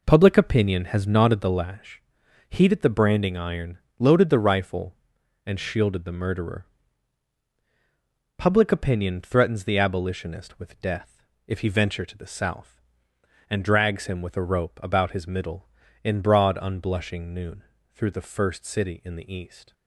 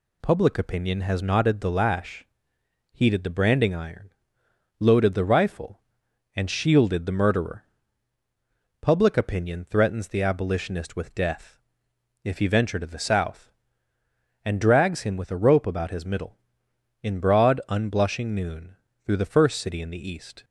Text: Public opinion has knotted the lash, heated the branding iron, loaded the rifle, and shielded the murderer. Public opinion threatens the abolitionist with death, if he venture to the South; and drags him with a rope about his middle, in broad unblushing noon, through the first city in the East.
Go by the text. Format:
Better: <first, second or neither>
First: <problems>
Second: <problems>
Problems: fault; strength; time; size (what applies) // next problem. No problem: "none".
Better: second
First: starts louder than the rest; noticeable; until 1.6 s; 4.5 dB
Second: none